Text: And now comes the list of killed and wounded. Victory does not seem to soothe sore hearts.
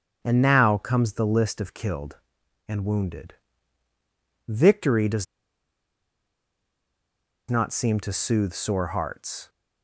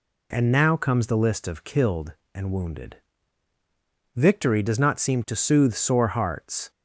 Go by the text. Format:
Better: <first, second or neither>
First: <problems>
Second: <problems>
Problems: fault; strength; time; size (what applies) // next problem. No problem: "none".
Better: second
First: starts louder than the rest; strong; until 1.2 s; 7 dB // pauses between "does" and "not"; strong; at 5.2 s; 2.2 s long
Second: none